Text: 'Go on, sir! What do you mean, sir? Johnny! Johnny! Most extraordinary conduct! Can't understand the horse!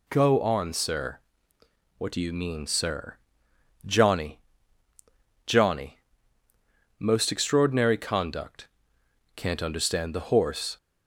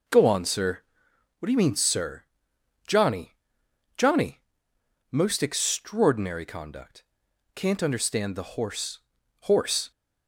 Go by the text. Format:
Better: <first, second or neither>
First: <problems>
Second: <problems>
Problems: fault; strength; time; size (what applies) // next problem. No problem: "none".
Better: first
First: none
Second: says "horse" twice; at 9.4 s